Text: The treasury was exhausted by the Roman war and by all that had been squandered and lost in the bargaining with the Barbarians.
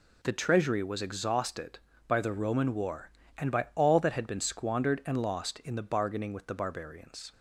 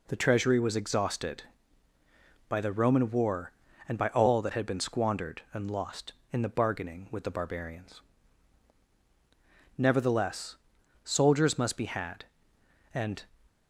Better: first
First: none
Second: goes on to say "Nevertheless soldiers must be had and"; strong; from 9.7 s on; 3.4 s long

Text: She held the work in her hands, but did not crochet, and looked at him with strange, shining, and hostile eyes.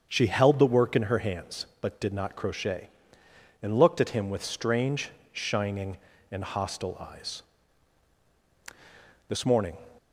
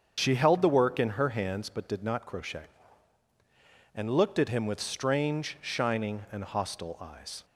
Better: second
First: starts louder than the rest; until 1.1 s; 7 dB // goes on to say "This morning"; from 9.2 s on; 0.50 s long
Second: starts louder than the rest; strong; until 1.1 s; 7 dB

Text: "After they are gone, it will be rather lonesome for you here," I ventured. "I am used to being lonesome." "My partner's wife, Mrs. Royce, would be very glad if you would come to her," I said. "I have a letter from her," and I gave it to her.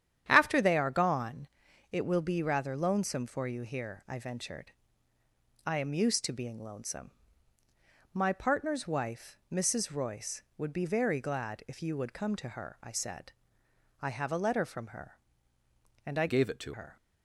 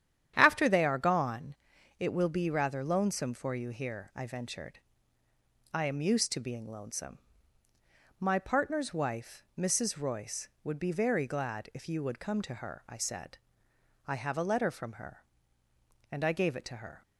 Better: second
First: starts louder than the rest; strong; until 1.2 s; 10 dB // changes voice from "gave" to "to"; from 16.2 to 16.7 s; 0.5 s long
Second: starts louder than the rest; strong; until 1.3 s; 10 dB

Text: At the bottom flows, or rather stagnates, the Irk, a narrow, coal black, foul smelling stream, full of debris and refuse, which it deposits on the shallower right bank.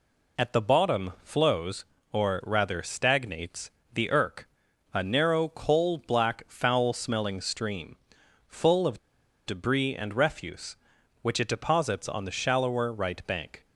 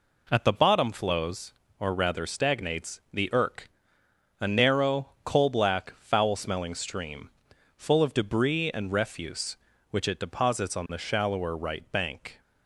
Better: second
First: pauses between "of" and "debris"; noticeable; at 8.9 s; 0.48 s long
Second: none

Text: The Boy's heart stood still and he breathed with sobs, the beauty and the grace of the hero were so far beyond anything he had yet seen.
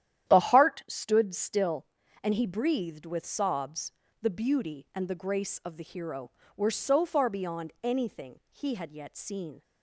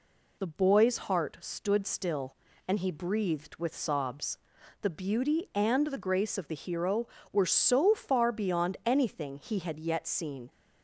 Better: second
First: starts louder than the rest; strong; until 1.3 s; 11 dB // skips "Boy's"; at 0.3 s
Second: none

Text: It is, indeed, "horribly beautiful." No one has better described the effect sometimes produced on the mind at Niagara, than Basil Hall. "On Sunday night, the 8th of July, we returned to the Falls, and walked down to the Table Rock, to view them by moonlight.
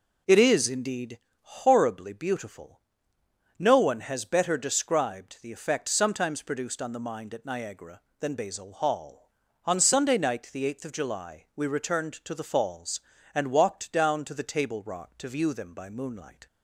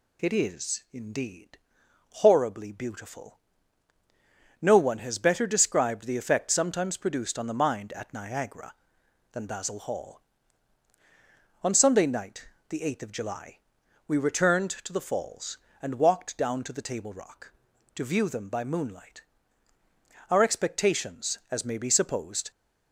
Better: first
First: none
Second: goes on to say "Our expectations as may be supposed"; strong; from 20.2 s on; 2.2 s long

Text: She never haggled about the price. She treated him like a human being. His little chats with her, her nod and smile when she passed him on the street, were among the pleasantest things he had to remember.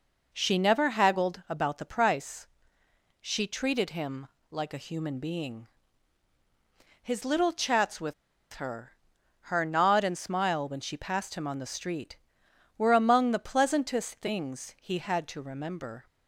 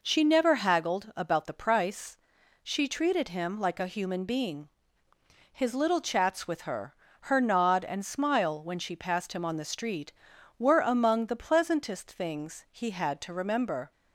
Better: second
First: pauses between "him" and "like"; slight; at 4.2 s; 0.22 s long // pauses between "with" and "her"; at 8.1 s; 0.40 s long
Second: none

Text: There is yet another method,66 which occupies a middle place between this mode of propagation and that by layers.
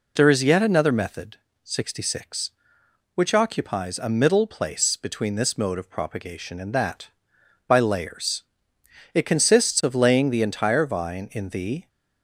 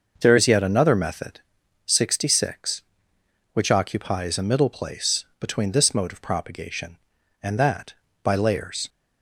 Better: second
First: goes on to say "It consists of laying the entire vine in the"; strong; from 9.1 s on; 2.7 s long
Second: none

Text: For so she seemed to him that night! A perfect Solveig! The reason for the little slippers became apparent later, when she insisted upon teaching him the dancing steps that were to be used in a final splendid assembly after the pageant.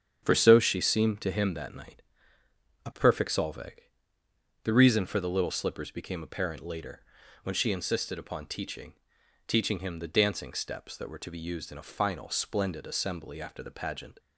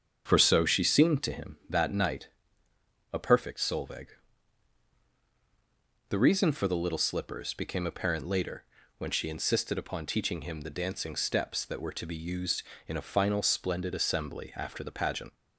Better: second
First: starts louder than the rest; strong; until 1.2 s; 8 dB // says "teaching" twice; at 9.4 s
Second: starts louder than the rest; strong; until 1.2 s; 7.5 dB

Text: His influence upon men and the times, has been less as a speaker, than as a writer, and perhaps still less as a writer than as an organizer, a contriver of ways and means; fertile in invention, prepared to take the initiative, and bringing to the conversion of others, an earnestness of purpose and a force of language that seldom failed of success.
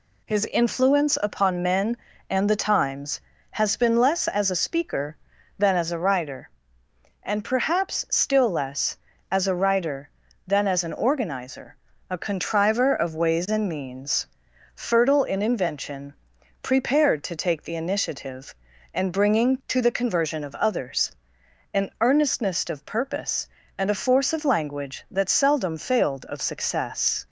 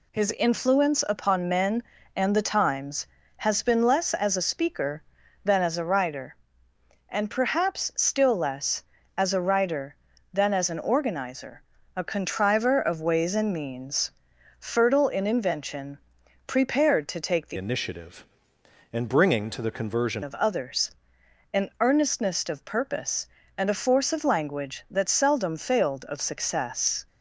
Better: first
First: none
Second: changes voice from "initiative" to "conversion"; from 17.5 to 20.2 s; 2.7 s long

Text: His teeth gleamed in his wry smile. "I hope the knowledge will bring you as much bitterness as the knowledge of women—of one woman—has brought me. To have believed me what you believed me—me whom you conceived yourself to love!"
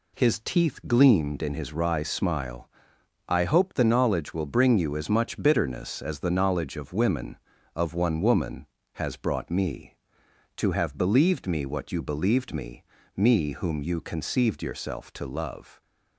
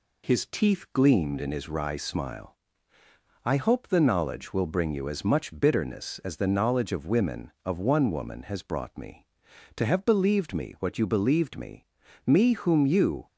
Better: first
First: none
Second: stops before "conceived yourself to love"; at 13.2 s

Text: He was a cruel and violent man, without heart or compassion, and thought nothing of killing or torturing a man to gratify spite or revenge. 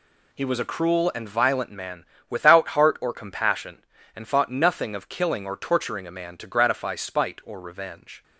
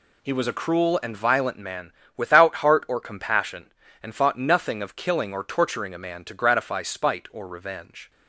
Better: neither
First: none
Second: none

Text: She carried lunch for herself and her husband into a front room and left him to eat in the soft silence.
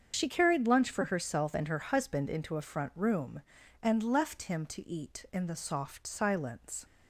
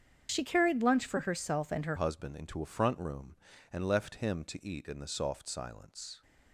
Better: first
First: starts louder than the rest; until 1.1 s; 7 dB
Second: starts louder than the rest; strong; until 1.3 s; 8 dB // changes voice at "husband"; from 1.9 s on; 4.3 s long

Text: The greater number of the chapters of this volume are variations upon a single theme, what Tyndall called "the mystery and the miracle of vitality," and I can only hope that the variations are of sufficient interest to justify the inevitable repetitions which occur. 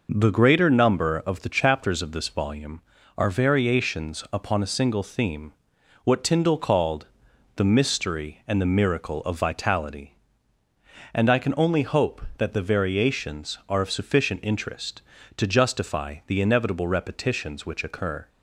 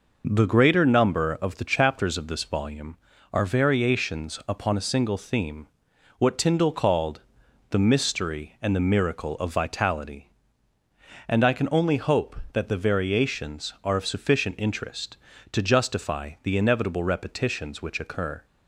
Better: neither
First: pauses between "called" and "the"; noticeable; at 7.0 s; 0.48 s long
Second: pauses between "called" and "the"; noticeable; at 7.2 s; 0.48 s long

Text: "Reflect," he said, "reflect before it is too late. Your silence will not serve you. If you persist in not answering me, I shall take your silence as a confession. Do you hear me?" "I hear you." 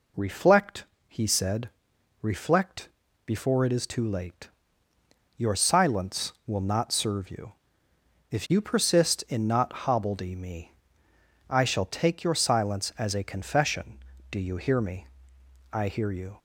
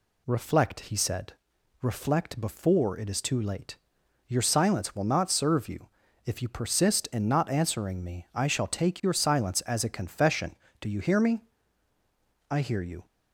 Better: second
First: pauses between "reflect" and "before"; slight; at 2.8 s; 0.36 s long // says "hobbledy" for "answering"; at 9.8 s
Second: none

